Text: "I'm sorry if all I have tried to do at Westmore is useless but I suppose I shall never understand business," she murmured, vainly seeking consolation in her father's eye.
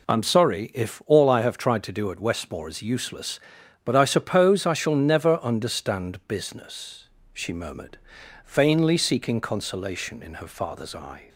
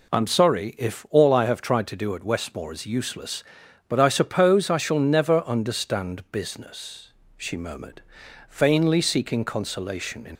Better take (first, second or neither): first